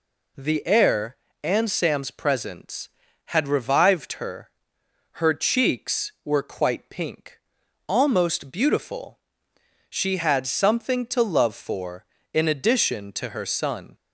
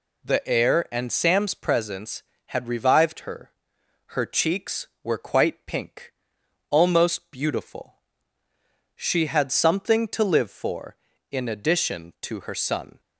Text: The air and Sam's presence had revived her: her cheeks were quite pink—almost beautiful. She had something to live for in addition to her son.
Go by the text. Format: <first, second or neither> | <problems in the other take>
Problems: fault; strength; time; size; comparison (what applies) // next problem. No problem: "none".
second | says "love" for "live"; at 11.2 s